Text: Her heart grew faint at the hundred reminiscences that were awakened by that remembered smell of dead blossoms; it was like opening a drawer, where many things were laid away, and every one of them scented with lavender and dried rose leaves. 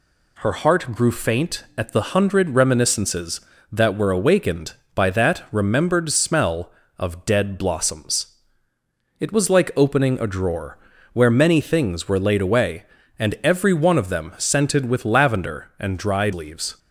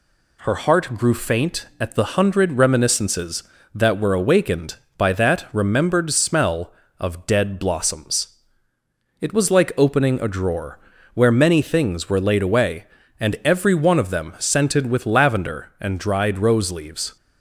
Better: second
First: skips "rose"; at 16.3 s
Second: none

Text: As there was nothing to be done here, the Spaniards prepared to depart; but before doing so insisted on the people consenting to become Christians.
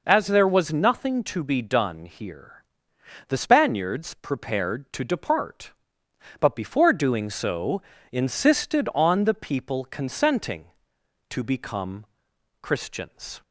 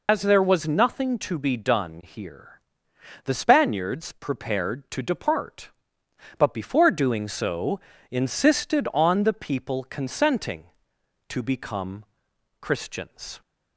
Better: first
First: pauses between "so" and "insisted"; slight; at 7.8 s; 0.31 s long // pauses between "become" and "Christians"; noticeable; at 12.0 s; 0.56 s long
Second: loses the start of "As"; at 0.0 s; 80 ms // pauses between "so" and "insisted"; slight; at 7.7 s; 0.32 s long // pauses between "become" and "Christians"; noticeable; at 12.0 s; 0.56 s long

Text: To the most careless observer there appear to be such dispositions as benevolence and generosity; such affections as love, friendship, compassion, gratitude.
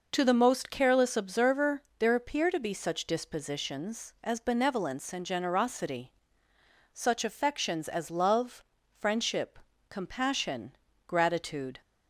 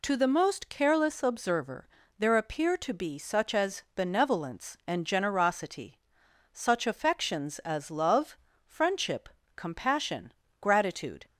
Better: first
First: pauses between "observer" and "there"; slight; at 1.8 s; 0.16 s long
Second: pauses between "observer" and "there"; slight; at 1.8 s; 0.30 s long // skips "dispositions"; at 3.5 s

